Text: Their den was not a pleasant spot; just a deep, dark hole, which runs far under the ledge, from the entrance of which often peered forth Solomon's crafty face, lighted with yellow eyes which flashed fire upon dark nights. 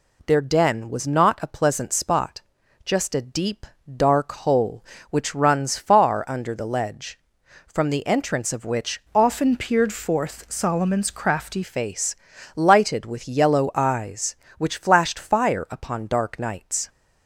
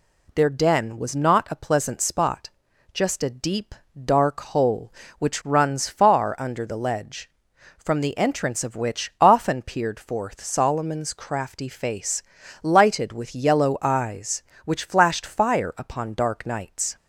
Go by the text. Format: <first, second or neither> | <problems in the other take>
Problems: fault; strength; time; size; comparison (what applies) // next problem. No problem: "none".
second | changes voice from "often" to "crafty"; from 9.1 to 11.6 s; 2.5 s long